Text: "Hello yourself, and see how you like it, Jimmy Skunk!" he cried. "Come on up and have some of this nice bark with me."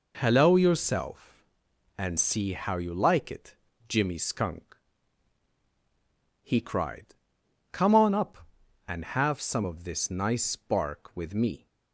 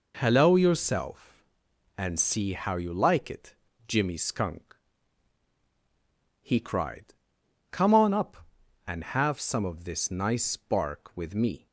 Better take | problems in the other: neither | none

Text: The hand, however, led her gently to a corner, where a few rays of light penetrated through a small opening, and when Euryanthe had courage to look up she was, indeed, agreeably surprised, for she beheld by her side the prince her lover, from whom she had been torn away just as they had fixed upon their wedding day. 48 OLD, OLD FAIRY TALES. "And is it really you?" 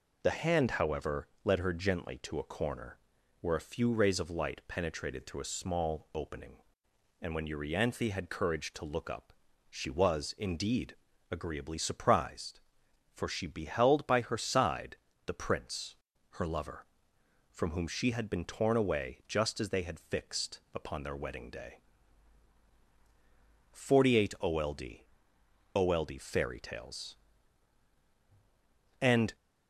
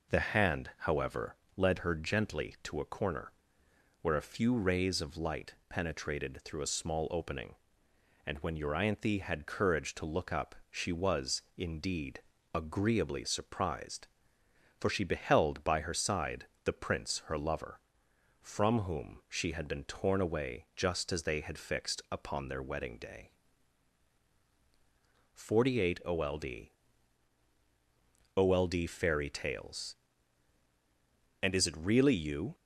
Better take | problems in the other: second | pauses between "up" and "she"; slight; at 9.3 s; 0.36 s long; slight in the second // pauses between "side" and "the"; slight; at 14.9 s; 0.32 s long; slight in the second // pauses between "prince" and "her"; slight; at 15.9 s; 0.36 s long // stops before "is it really you"; at 29.3 s

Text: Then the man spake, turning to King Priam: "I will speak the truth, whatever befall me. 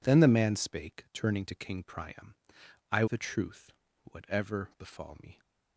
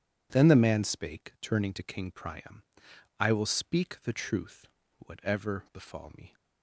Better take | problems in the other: second | skips "will speak"; at 3.0 s

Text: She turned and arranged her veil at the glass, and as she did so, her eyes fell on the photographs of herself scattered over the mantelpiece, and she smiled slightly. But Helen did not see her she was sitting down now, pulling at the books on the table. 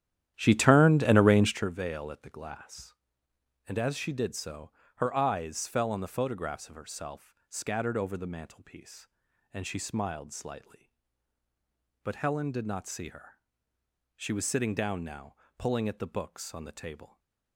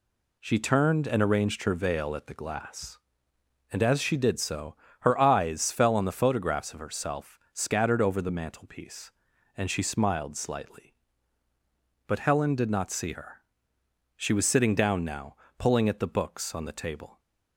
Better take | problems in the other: second | starts louder than the rest; strong; until 1.7 s; 11.5 dB // pauses between "her" and "she"; noticeable; at 13.3 s; 0.78 s long; noticeable in the second

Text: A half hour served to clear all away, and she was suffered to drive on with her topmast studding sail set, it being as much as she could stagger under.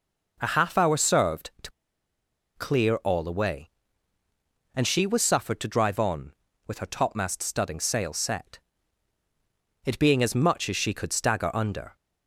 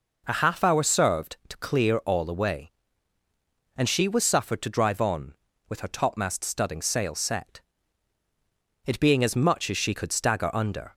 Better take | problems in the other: second | pauses between "to" and "clear"; noticeable; at 1.7 s; 0.85 s long

